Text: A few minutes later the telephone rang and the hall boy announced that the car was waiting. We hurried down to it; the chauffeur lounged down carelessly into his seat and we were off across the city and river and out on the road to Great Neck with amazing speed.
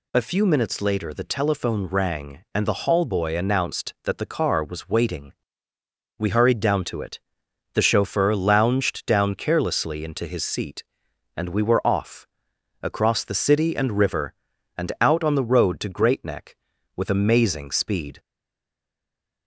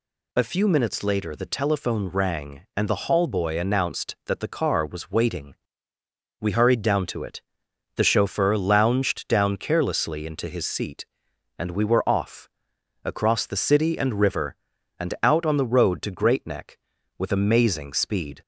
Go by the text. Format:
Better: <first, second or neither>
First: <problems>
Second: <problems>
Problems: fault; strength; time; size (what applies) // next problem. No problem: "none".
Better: second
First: pauses between "off" and "across"; noticeable; at 12.2 s; 0.56 s long // stays silent after the last word; noticeable; from 18.1 s on; 1.3 s long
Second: pauses between "off" and "across"; noticeable; at 12.4 s; 0.56 s long